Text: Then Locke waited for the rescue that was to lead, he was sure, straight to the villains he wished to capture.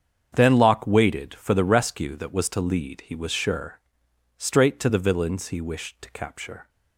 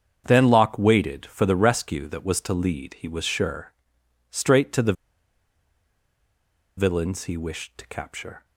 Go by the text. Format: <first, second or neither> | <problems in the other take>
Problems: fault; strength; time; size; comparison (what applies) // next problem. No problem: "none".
first | starts louder than the rest; strong; until 1.2 s; 7.5 dB; strong in the first // pauses between "the" and "villains"; strong; at 4.9 s; 1.8 s long